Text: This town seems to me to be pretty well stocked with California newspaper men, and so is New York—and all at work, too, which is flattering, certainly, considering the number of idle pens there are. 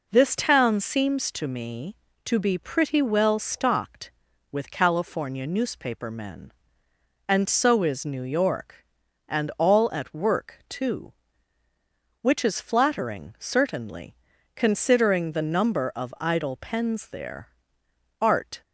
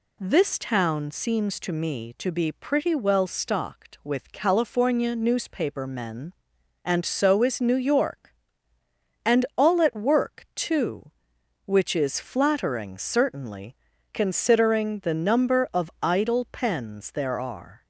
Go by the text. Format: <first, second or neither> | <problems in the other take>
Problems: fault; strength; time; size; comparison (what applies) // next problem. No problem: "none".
second | says "art" for "are"; at 18.2 s